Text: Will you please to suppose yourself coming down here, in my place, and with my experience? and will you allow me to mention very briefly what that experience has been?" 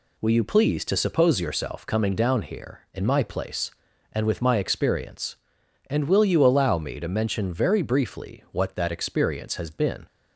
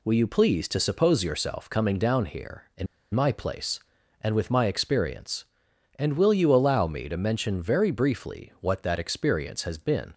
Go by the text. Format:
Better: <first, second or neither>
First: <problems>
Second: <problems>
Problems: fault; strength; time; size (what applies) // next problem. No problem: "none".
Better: first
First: none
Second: pauses between "in" and "my"; slight; at 2.8 s; 0.27 s long